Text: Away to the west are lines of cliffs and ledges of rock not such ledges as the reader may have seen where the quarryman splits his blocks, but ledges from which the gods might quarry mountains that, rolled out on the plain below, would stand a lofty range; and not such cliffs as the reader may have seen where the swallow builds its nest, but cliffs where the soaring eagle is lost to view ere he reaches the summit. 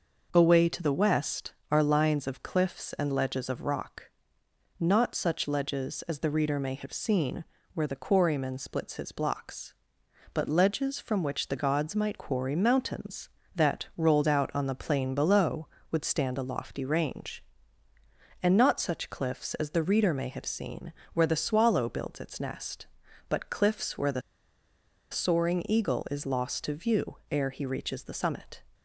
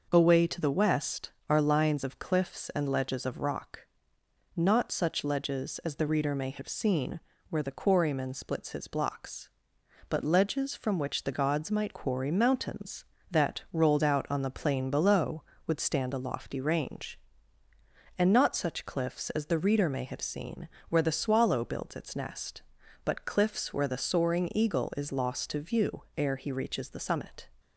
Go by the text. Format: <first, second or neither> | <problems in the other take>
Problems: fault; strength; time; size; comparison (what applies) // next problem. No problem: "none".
second | pauses between "rock" and "not"; noticeable; at 4.0 s; 0.76 s long; noticeable in the second // pauses between "seen" and "where"; slight; at 7.4 s; 0.32 s long; slight in the second // pauses between "seen" and "where"; slight; at 20.9 s; 0.22 s long; slight in the second // pauses between "the" and "soaring"; noticeable; at 24.2 s; 0.91 s long